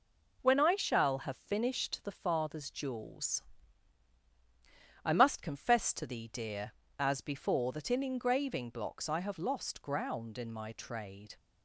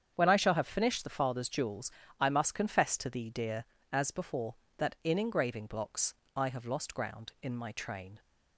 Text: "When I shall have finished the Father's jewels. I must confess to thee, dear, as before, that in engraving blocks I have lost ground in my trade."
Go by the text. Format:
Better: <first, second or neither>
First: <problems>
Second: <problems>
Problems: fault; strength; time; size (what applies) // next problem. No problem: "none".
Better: first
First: none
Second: starts louder than the rest; strong; until 1.1 s; 8 dB // pauses between "blocks" and "I"; slight; at 6.1 s; 0.22 s long // says "train" for "trade"; at 7.7 s